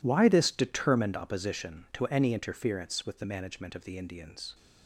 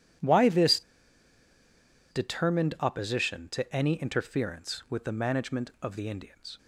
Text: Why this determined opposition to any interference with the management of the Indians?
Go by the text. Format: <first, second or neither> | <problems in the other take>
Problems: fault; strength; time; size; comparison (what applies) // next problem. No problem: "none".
first | pauses between "this" and "determined"; strong; at 0.8 s; 1.2 s long